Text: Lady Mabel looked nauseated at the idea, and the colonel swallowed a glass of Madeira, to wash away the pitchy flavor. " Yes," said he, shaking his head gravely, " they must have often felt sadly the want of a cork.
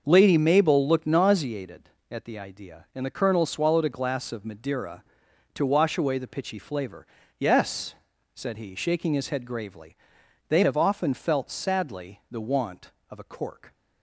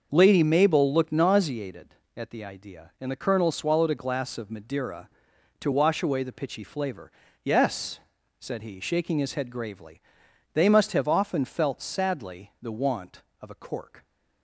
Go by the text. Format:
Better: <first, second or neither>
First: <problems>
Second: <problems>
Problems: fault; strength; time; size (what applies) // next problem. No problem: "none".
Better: second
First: starts louder than the rest; noticeable; until 1.0 s; 6 dB // skips "must"; at 10.6 s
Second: starts louder than the rest; noticeable; until 1.1 s; 6 dB